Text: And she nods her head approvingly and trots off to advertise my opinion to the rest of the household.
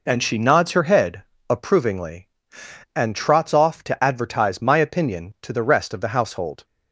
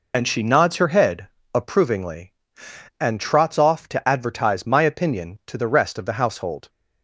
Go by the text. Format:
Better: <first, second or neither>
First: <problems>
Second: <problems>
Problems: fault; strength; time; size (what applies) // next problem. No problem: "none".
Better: first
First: pauses between "head" and "approvingly"; slight; at 1.2 s; 0.24 s long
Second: loses the start of "And"; at 0.1 s; 35 ms // pauses between "head" and "approvingly"; slight; at 1.2 s; 0.24 s long